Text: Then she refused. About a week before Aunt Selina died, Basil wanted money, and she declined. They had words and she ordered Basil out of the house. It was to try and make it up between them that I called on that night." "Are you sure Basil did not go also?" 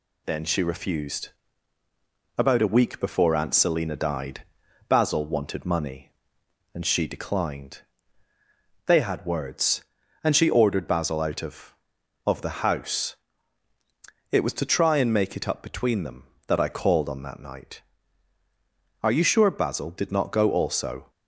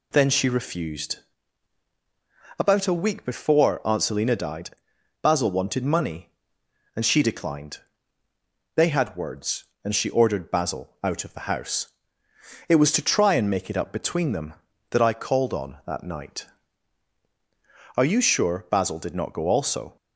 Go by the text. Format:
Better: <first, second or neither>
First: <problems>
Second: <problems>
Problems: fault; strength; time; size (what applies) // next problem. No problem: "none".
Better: second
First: says "of" twice; at 12.2 s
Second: none